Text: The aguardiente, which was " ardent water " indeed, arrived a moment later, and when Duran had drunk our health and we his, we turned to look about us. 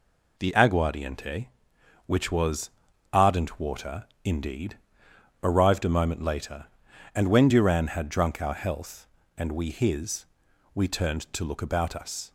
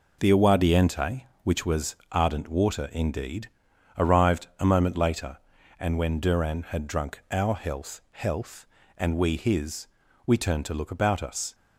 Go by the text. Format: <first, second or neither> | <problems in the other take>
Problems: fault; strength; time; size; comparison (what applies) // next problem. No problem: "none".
first | says "health" twice; at 8.1 s